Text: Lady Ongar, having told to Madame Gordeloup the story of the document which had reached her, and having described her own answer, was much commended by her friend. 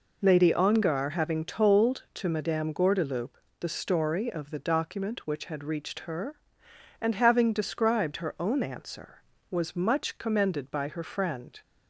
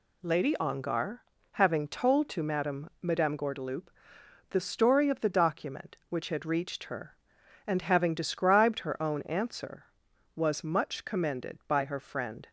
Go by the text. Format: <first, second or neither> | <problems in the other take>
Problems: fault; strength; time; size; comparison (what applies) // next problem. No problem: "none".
first | says "Madame" twice; at 3.0 s // pauses between "Gordeloup" and "the"; noticeable; at 3.8 s; 0.62 s long; slight in the first